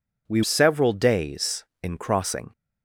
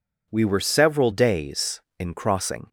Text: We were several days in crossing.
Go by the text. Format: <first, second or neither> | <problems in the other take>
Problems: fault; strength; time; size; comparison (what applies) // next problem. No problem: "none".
second | skips "were"; at 0.4 s